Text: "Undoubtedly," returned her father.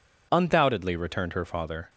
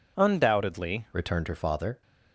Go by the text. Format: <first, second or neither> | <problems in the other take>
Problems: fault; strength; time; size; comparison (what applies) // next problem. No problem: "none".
first | changes voice at "returned"; from 1.1 s on; 0.9 s long